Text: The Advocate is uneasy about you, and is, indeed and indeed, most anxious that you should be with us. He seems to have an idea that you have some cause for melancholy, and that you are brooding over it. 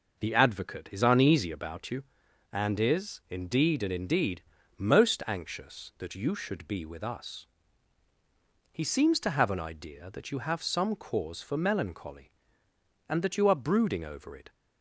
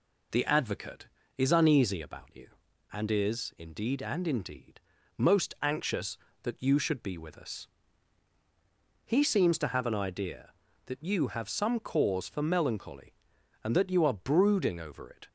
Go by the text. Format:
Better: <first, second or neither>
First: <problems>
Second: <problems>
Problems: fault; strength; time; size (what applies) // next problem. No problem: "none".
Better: neither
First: none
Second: none